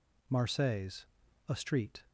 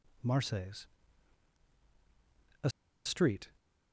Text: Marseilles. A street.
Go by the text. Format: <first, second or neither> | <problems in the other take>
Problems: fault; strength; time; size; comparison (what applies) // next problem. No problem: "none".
first | pauses between "A" and "street"; slight; at 2.6 s; 0.35 s long